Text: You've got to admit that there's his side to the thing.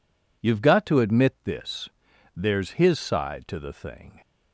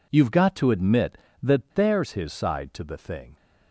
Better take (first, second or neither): second